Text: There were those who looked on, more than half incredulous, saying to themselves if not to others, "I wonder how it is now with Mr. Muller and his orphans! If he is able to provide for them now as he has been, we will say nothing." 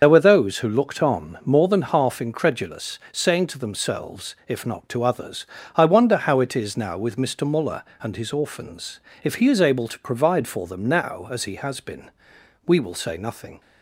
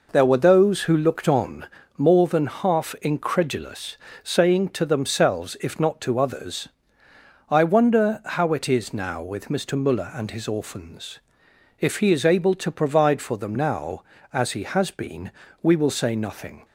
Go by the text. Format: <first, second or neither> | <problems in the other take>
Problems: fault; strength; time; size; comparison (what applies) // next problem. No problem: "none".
second | loses the start of "There"; at 0.0 s; 60 ms // starts louder than the rest; until 1.0 s; 6 dB